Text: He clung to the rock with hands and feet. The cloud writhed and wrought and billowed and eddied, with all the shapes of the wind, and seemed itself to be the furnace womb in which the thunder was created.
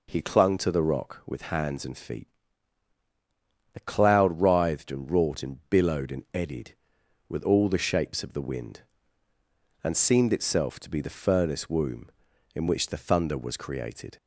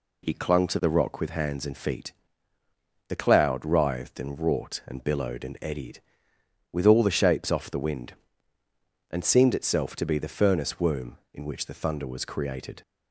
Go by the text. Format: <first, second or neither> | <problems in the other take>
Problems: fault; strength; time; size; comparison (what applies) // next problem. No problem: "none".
first | says "off" for "of"; at 7.5 s